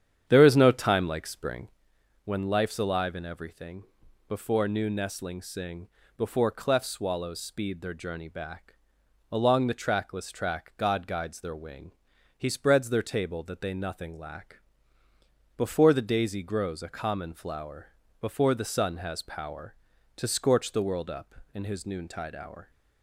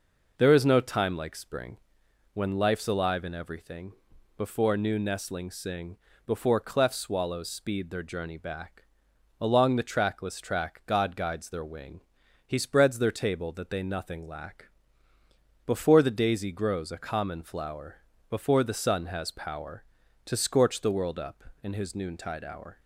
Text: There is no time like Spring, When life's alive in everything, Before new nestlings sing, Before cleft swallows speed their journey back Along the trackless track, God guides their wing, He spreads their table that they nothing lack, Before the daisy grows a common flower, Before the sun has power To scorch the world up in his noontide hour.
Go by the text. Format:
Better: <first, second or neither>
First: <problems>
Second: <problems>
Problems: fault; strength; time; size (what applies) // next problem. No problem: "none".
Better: second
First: starts louder than the rest; strong; until 1.8 s; 9 dB // pauses between "back" and "Along"; noticeable; at 8.7 s; 0.52 s long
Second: pauses between "back" and "Along"; noticeable; at 8.8 s; 0.52 s long